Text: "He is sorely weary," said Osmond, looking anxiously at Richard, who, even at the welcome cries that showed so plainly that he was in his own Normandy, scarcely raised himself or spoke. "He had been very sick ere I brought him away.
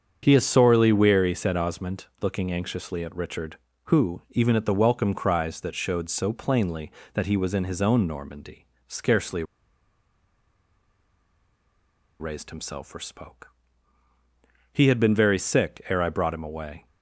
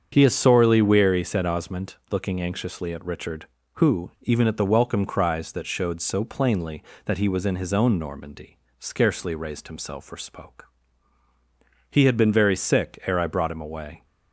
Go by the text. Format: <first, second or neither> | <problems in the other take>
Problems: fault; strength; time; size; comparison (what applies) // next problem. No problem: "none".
second | starts louder than the rest; until 1.2 s; 7 dB; also in the second // pauses between "scarcely" and "raised"; strong; at 9.4 s; 2.7 s long